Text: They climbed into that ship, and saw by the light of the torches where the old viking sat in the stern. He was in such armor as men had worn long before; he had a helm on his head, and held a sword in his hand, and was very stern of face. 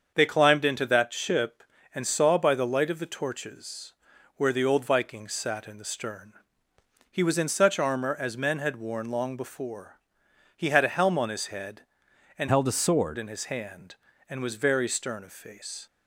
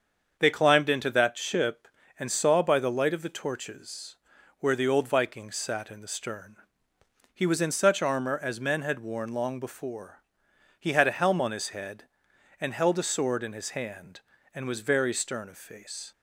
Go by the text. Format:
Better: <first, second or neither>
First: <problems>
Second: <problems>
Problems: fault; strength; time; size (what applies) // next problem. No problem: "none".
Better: second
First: starts louder than the rest; until 1.1 s; 7 dB // pauses between "torches" and "where"; at 3.9 s; 0.44 s long // changes voice from "held" to "sword"; from 12.4 to 13.1 s; 0.7 s long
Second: starts louder than the rest; until 1.4 s; 7 dB // pauses between "torches" and "where"; at 4.1 s; 0.44 s long